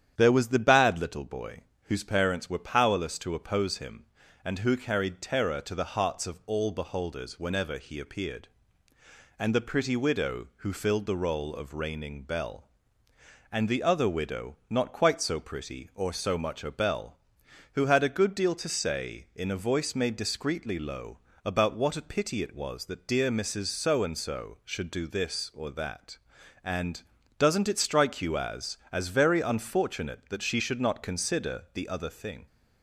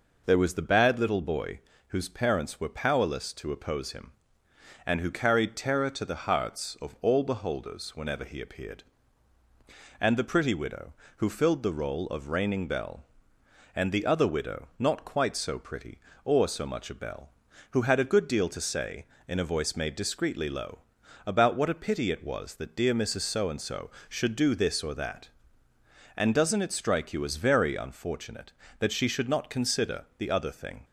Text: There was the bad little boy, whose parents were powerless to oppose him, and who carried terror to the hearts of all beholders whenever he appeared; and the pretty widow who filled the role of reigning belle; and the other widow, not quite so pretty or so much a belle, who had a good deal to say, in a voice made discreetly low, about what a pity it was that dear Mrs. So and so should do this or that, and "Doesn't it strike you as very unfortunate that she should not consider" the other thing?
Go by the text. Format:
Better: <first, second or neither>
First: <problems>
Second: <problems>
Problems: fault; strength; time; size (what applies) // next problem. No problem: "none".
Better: second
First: starts louder than the rest; strong; until 1.1 s; 9.5 dB // pauses between "and" and "Doesn't"; slight; at 27.0 s; 0.36 s long // says "as" twice; at 28.9 s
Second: none